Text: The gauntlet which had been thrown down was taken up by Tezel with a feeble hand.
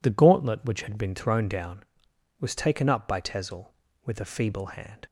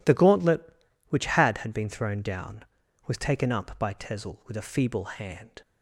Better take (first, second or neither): first